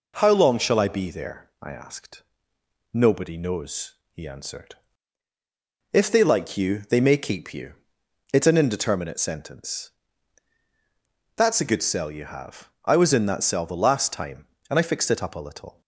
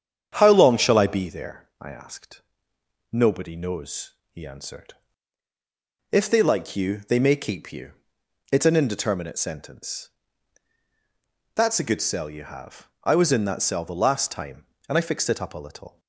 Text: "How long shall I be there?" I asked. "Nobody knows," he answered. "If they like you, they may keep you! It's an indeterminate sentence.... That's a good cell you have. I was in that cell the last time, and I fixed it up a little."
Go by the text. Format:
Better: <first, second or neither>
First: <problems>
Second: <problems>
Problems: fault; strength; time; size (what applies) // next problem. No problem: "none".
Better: first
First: none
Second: starts louder than the rest; strong; until 1.3 s; 8.5 dB